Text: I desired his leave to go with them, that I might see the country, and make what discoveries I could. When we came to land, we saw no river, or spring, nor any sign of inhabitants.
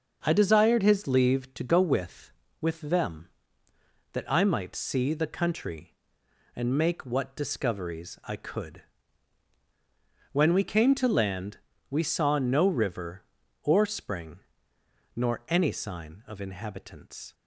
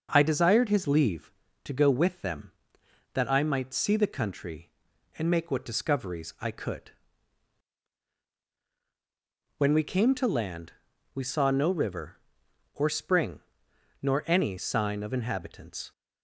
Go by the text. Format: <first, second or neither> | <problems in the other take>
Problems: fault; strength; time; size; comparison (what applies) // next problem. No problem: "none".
second | starts louder than the rest; until 1.2 s; 6.5 dB // says "with" twice; at 2.5 s